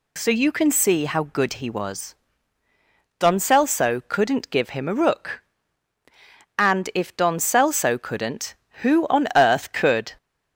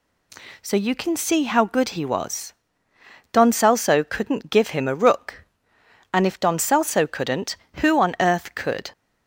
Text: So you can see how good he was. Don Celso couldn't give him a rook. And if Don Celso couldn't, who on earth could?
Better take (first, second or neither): neither